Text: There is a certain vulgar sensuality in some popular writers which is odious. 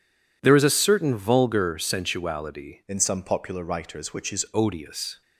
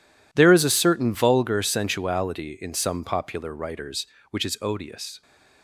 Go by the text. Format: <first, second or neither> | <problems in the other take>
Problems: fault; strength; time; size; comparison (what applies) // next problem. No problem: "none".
second | changes voice from "in" to "is"; from 2.8 to 4.4 s; 1.6 s long